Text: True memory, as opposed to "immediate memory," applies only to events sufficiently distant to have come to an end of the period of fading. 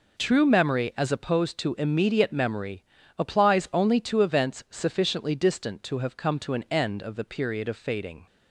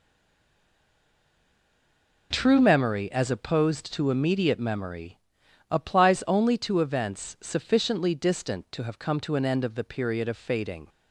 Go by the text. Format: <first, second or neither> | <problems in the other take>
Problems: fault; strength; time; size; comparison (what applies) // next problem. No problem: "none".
first | stays silent before the first word; until 2.3 s; 2.3 s long